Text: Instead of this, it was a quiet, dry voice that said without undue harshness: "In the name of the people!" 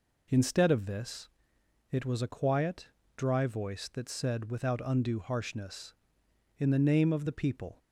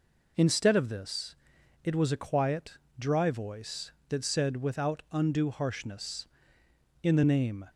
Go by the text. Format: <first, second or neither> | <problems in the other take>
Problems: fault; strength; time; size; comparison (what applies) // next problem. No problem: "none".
first | stops before "of the people"; at 7.7 s